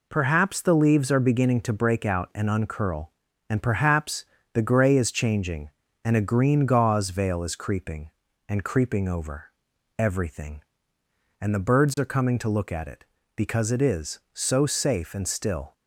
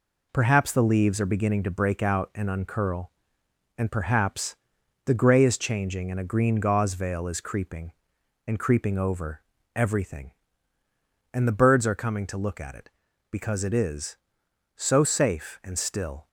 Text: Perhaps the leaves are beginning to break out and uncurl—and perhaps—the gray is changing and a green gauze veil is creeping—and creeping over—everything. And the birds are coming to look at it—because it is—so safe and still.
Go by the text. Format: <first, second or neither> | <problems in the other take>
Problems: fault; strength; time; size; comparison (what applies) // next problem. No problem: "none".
neither | none